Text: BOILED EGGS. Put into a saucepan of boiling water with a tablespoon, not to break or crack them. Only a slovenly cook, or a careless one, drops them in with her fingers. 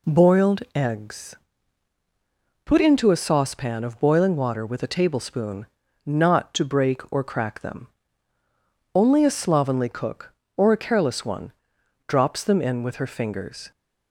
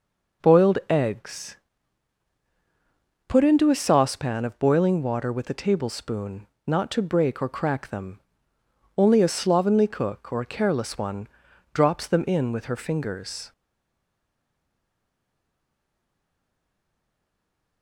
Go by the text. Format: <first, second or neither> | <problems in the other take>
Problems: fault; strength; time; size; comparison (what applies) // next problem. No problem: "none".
first | stays silent after the last word; strong; from 13.5 s on; 4.3 s long